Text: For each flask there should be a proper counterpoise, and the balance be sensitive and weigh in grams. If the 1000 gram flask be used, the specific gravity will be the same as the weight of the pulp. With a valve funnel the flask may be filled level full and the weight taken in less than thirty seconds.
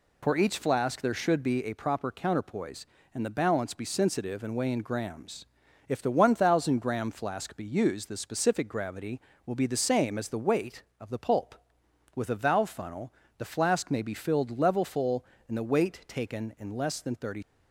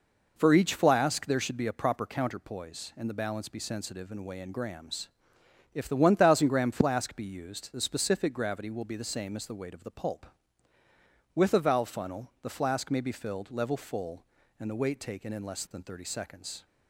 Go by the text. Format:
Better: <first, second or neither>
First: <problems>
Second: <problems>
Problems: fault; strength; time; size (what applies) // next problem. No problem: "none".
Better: second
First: pauses between "funnel" and "the"; slight; at 13.1 s; 0.26 s long // stops before "seconds"; at 17.4 s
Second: none